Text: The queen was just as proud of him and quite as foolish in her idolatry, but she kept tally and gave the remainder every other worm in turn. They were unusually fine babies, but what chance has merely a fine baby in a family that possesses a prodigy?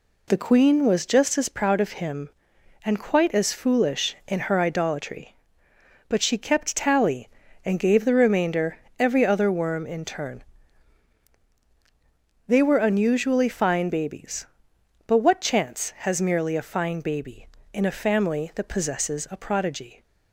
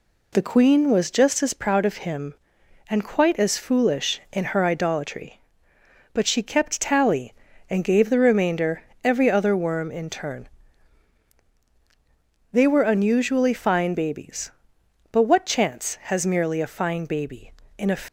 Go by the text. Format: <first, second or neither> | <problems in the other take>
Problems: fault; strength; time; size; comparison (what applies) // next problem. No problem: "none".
first | pauses between "remainder" and "every"; slight; at 8.8 s; 0.22 s long; slight in the first // stops before "family that possesses a prodigy"; at 18.0 s